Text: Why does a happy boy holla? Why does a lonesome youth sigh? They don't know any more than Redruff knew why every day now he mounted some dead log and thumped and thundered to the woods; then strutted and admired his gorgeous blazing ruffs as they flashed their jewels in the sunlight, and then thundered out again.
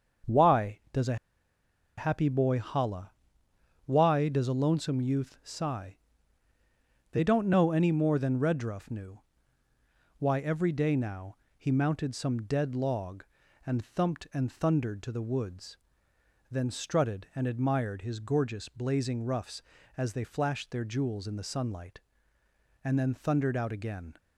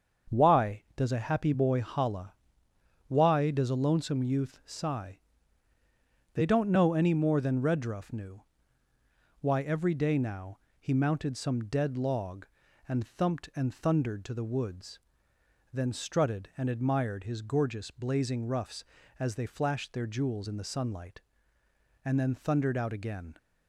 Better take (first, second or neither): second